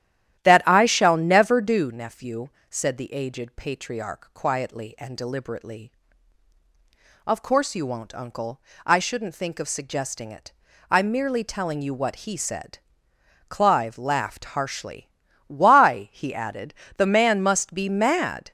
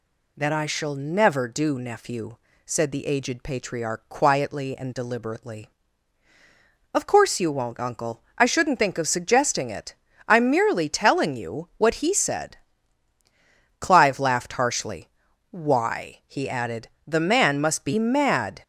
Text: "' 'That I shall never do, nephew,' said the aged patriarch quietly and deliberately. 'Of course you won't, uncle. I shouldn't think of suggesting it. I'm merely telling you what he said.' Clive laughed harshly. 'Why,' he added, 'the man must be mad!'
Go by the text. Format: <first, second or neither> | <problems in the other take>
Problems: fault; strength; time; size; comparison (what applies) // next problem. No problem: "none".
second | starts louder than the rest; strong; until 2.0 s; 12 dB